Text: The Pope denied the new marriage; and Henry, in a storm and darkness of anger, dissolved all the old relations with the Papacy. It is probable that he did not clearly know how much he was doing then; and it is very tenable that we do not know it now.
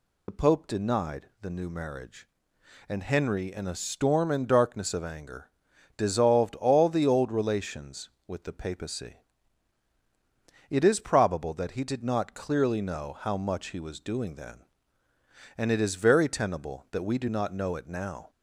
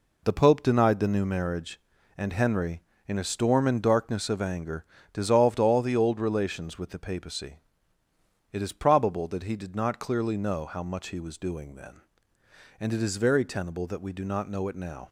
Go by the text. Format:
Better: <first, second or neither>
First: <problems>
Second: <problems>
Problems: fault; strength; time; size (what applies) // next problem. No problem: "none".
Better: second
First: loses the start of "The"; at 0.2 s; 40 ms // pauses between "denied" and "the"; slight; at 1.2 s; 0.16 s long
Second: none